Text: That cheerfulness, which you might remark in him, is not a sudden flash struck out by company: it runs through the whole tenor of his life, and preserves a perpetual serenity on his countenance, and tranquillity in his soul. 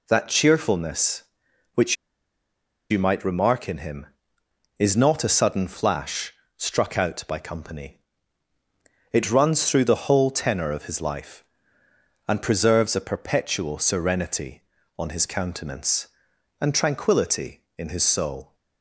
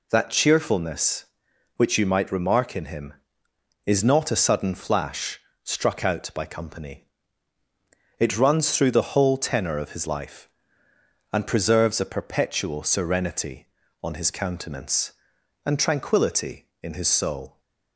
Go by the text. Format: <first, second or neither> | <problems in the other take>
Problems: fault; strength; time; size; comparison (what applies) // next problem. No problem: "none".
second | pauses between "which" and "you"; noticeable; at 1.9 s; 0.95 s long // pauses between "flash" and "struck"; slight; at 6.3 s; 0.24 s long; slight in the second